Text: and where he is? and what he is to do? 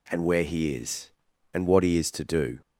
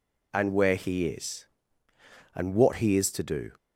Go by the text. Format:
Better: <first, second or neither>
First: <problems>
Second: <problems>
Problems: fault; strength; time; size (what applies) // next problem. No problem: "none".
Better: neither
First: none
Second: none